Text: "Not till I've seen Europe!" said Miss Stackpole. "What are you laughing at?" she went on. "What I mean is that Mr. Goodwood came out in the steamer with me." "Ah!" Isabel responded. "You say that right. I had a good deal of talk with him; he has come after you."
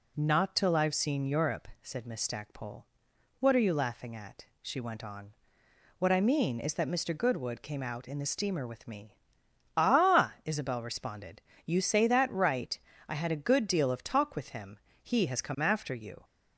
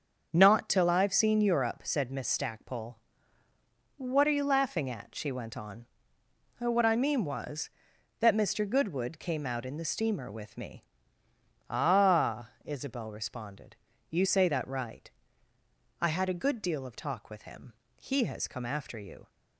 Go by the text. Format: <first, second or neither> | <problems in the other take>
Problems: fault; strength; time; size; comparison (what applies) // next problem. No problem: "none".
first | starts louder than the rest; until 1.3 s; 6.5 dB // says "was" for "is"; at 7.2 s